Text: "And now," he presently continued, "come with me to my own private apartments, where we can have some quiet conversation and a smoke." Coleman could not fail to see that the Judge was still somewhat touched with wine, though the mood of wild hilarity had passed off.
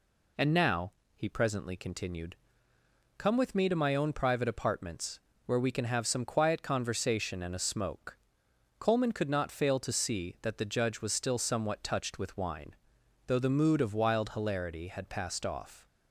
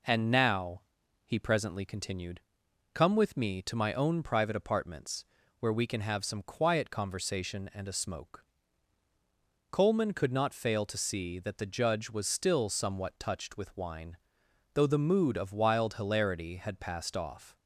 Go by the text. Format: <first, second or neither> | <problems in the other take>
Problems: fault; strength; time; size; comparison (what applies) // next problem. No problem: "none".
neither | none